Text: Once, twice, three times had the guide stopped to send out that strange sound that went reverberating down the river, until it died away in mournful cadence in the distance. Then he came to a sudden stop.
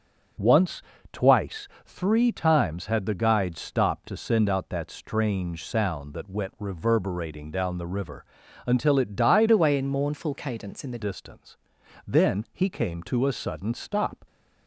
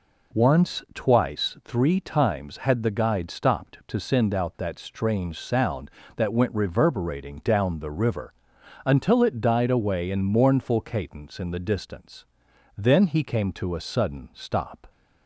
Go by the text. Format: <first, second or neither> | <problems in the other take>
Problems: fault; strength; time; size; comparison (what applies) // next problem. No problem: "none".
second | starts louder than the rest; noticeable; until 1.8 s; 6 dB // changes voice from "away" to "the"; from 9.4 to 10.9 s; 1.5 s long